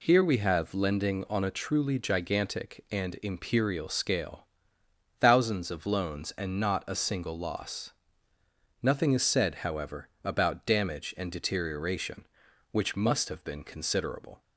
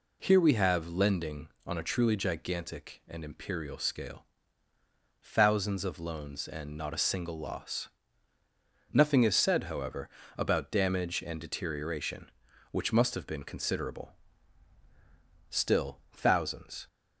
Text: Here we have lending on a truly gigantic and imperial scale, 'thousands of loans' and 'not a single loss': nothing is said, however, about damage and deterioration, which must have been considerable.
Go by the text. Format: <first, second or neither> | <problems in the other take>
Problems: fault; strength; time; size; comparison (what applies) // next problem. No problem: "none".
first | goes on to say "Still thousands"; from 15.4 s on; 1.3 s long